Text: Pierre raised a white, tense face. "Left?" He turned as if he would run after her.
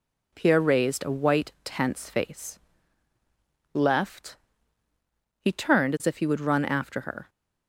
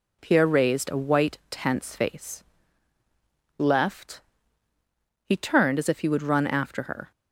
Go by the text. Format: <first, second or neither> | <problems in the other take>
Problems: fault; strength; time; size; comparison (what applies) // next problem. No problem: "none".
neither | none